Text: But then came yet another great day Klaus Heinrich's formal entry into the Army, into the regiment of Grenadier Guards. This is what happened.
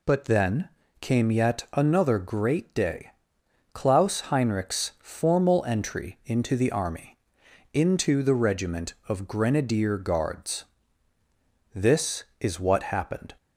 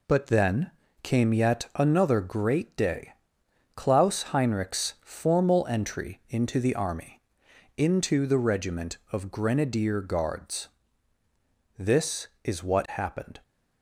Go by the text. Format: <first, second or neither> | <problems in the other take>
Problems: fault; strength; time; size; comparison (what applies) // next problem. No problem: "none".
first | gets quieter; noticeable; throughout; 5 dB // pauses between "then" and "came"; slight; at 0.7 s; 0.32 s long; slight in the first // pauses between "day" and "Klaus"; noticeable; at 3.1 s; 0.62 s long; noticeable in the first